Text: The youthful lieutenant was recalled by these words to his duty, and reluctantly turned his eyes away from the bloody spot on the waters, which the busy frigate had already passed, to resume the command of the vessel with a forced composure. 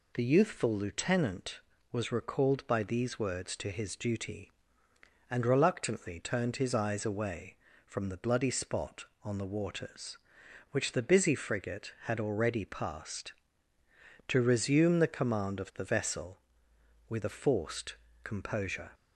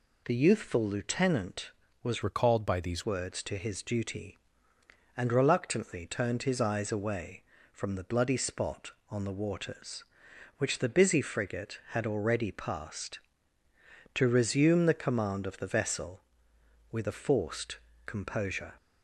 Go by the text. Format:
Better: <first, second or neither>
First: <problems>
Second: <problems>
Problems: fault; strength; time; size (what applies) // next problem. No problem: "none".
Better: first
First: pauses between "forced" and "composure"; slight; at 17.9 s; 0.28 s long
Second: changes voice from "recalled" to "these"; from 2.2 to 3.0 s; 0.8 s long // pauses between "forced" and "composure"; slight; at 17.7 s; 0.28 s long